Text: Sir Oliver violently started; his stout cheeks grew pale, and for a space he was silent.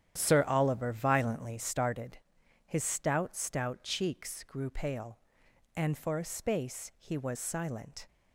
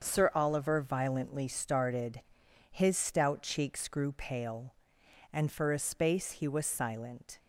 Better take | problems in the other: second | starts louder than the rest; strong; until 1.1 s; 10 dB; also in the second // says "stout" twice; at 3.3 s

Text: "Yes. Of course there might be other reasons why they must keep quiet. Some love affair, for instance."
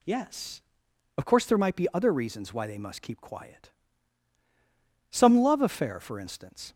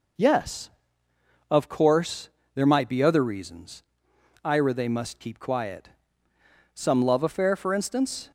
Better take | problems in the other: first | pauses between "course" and "there"; slight; at 2.2 s; 0.26 s long // says "ira" for "why"; at 4.4 s

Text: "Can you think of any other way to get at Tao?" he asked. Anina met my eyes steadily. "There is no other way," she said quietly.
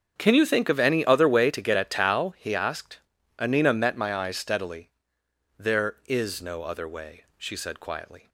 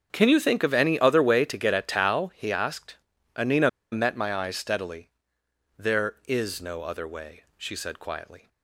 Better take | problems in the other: first | starts louder than the rest; until 1.1 s; 7 dB; also in the first // pauses between "Anina" and "met"; slight; at 3.6 s; 0.22 s long

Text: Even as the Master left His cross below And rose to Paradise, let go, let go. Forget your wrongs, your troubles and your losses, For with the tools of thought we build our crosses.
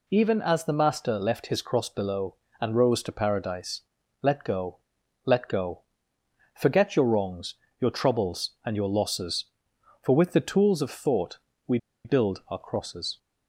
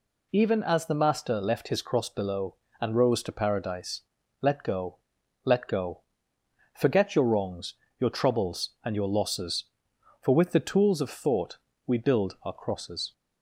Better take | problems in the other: second | pauses between "thought" and "we"; slight; at 11.3 s; 0.28 s long; slight in the second // pauses between "we" and "build"; slight; at 11.7 s; 0.27 s long

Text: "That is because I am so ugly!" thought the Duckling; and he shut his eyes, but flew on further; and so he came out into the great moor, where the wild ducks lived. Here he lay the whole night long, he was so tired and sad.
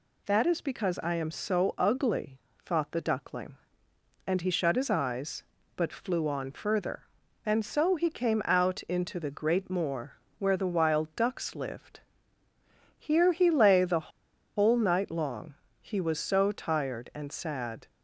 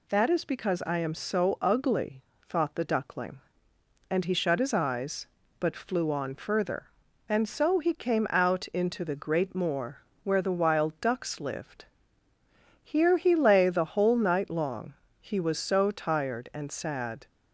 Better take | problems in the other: second | pauses between "the" and "whole"; noticeable; at 14.1 s; 0.46 s long

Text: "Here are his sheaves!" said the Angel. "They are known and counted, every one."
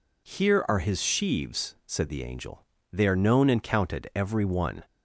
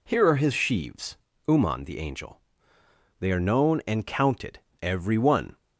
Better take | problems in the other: first | says "uman" for "said"; at 1.4 s

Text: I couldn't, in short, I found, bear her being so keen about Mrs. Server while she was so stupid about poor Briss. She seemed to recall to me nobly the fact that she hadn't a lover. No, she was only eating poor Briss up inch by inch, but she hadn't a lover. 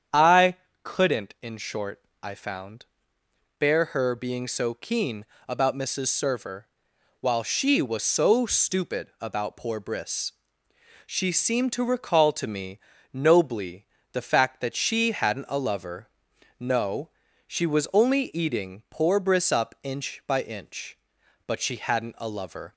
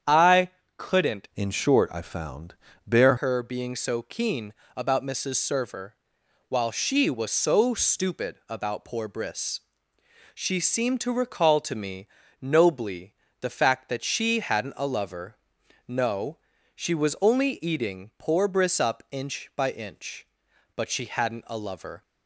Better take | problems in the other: first | starts louder than the rest; strong; until 1.4 s; 8.5 dB; strong in the first // pauses between "I" and "couldn't"; slight; at 0.4 s; 0.26 s long; slight in the first // changes voice from "in" to "bear"; from 1.3 to 3.1 s; 1.8 s long // pauses between "keen" and "about"; slight; at 4.5 s; 0.22 s long; slight in the first // pauses between "Server" and "while"; noticeable; at 5.9 s; 0.56 s long; noticeable in the first // pauses between "me" and "nobly"; slight; at 12.0 s; 0.34 s long; slight in the first // pauses between "nobly" and "the"; slight; at 13.1 s; 0.28 s long; slight in the first

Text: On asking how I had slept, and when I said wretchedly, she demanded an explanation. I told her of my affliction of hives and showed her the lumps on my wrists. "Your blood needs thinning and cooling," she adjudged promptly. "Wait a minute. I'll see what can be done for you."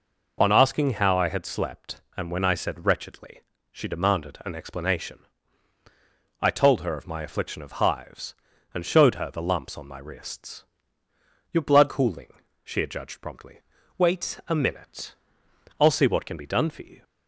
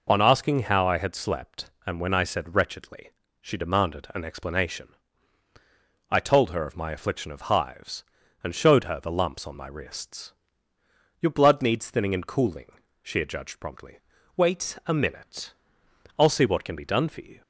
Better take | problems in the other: second | skips "needs thinning and"; at 11.8 s

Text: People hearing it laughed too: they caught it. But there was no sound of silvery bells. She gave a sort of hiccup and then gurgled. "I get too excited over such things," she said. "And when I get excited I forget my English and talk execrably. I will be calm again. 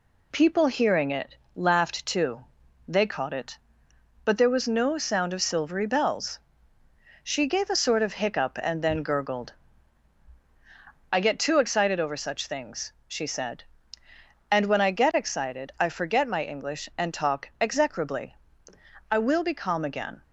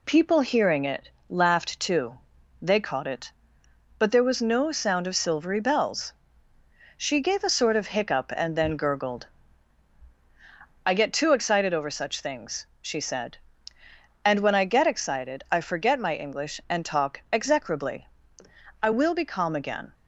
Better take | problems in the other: neither | pauses between "it" and "laughed"; slight; the same in both

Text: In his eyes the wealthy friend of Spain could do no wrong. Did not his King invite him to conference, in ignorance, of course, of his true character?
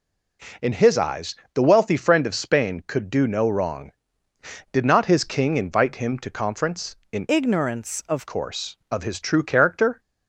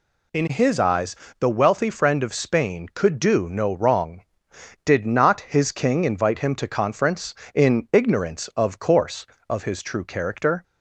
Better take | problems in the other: second | pauses between "eyes" and "the"; slight; at 1.3 s; 0.18 s long; slight in the second // changes voice from "ignorance" to "of"; from 7.2 to 8.2 s; 1.0 s long

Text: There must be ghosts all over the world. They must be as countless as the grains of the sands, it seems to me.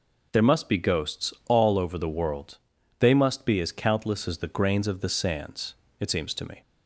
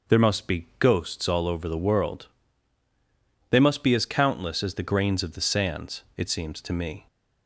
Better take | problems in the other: neither | none

